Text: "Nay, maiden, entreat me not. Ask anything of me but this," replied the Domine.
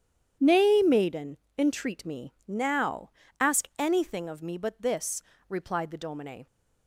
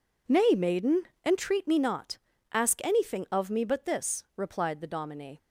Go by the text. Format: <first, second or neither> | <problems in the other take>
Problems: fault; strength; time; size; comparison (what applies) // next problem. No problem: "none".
second | starts louder than the rest; strong; until 1.6 s; 9.5 dB // says "now" for "not"; at 2.4 s